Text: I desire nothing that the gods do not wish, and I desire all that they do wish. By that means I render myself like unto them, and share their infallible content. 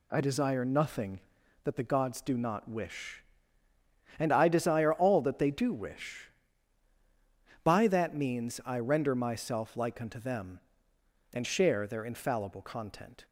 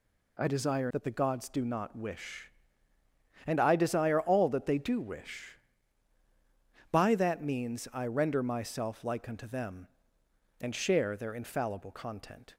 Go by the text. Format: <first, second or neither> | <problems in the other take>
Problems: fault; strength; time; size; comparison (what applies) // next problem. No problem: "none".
first | skips "nothing"; at 0.9 s